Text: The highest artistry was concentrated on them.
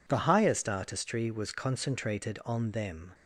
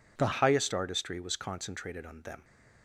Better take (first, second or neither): first